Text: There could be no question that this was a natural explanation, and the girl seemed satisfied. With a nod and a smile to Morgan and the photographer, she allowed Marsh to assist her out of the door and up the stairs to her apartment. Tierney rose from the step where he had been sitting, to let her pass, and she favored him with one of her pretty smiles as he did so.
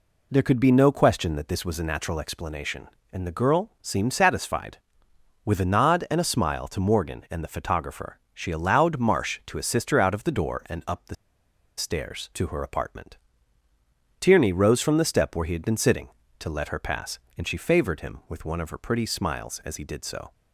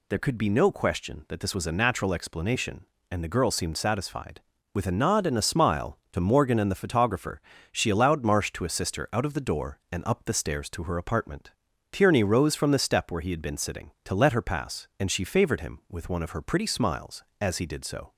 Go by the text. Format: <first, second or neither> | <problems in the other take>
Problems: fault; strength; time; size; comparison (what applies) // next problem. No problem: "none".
second | pauses between "the" and "stairs"; noticeable; at 11.1 s; 0.63 s long